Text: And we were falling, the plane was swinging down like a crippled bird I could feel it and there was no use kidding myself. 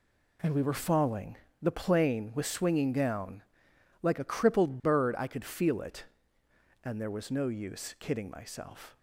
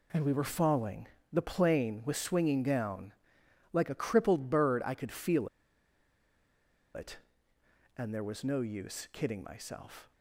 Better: first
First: pauses between "down" and "like"; noticeable; at 3.4 s; 0.60 s long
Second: pauses between "down" and "like"; noticeable; at 3.1 s; 0.60 s long // pauses between "feel" and "it"; strong; at 5.4 s; 1.4 s long

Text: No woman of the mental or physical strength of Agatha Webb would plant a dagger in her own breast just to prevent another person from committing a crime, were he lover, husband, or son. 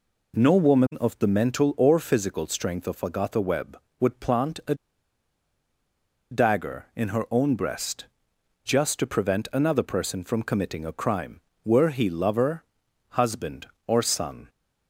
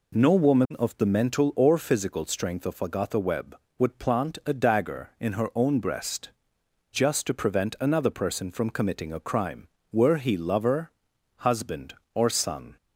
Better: second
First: pauses between "a" and "dagger"; strong; at 4.7 s; 1.5 s long // pauses between "breast" and "just"; noticeable; at 8.0 s; 0.58 s long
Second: pauses between "breast" and "just"; noticeable; at 6.2 s; 0.61 s long

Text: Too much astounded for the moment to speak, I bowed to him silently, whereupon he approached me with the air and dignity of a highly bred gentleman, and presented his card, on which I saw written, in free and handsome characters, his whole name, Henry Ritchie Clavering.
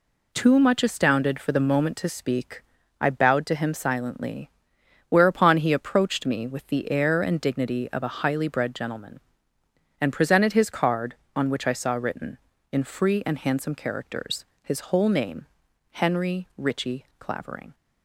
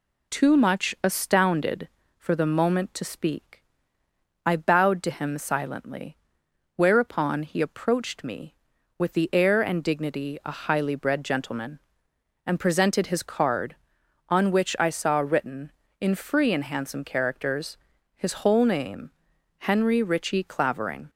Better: first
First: none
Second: skips "of"; at 10.4 s

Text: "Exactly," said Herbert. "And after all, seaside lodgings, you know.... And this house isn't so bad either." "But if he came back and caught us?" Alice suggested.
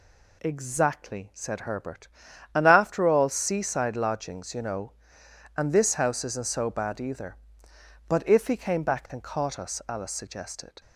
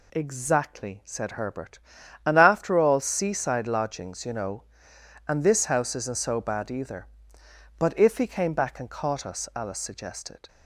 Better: neither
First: none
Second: none

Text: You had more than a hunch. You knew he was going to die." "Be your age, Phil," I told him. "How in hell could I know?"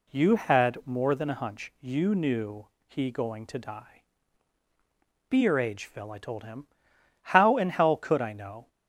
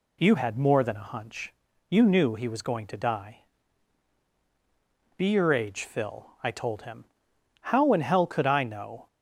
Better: second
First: pauses between "knew" and "he"; slight; at 2.6 s; 0.20 s long // skips "was"; at 3.1 s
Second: none

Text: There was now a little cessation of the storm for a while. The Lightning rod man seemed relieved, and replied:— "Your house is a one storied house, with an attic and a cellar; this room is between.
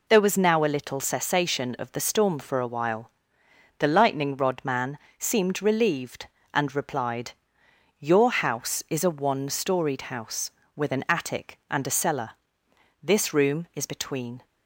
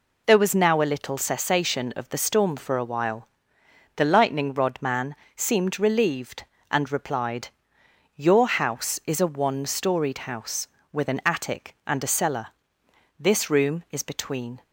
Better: neither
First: pauses between "man" and "seemed"; slight; at 4.9 s; 0.20 s long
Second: pauses between "man" and "seemed"; slight; at 5.1 s; 0.20 s long

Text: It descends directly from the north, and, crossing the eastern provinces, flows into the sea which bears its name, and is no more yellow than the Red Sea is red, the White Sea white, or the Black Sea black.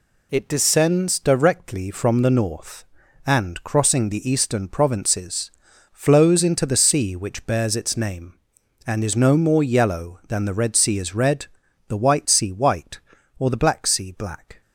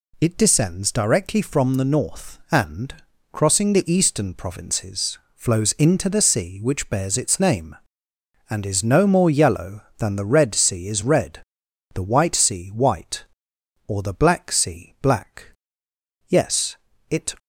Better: first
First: none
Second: goes on to say "Yes it"; noticeable; from 16.2 s on; 1.0 s long

